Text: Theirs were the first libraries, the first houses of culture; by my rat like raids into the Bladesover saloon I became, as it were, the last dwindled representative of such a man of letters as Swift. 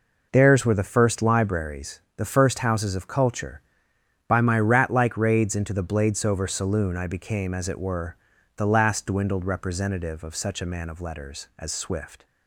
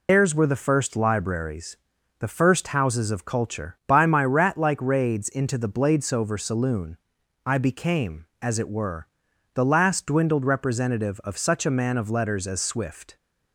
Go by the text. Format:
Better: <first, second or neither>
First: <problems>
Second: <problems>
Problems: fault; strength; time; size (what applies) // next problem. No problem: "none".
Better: first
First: none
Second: loses the start of "Theirs"; at 0.0 s; 90 ms // pauses between "saloon" and "I"; noticeable; at 6.9 s; 0.48 s long